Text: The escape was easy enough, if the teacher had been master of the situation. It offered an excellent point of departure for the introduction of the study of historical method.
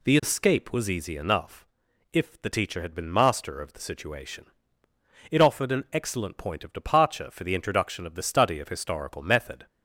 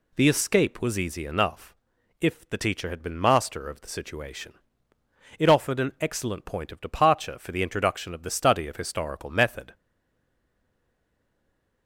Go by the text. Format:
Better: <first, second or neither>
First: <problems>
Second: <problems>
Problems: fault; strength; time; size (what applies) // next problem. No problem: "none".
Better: first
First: none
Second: stays silent after the last word; from 9.7 s on; 2.1 s long